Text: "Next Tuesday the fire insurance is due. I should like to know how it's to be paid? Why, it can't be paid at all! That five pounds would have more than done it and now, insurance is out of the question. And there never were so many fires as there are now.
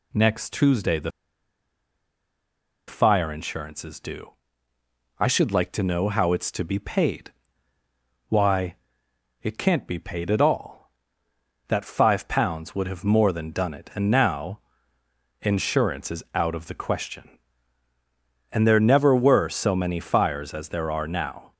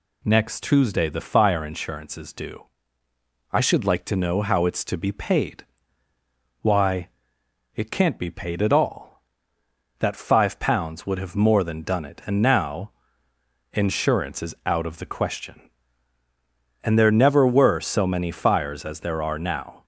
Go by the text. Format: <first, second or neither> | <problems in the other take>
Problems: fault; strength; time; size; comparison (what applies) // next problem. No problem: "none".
second | pauses between "the" and "fire"; strong; at 1.0 s; 1.7 s long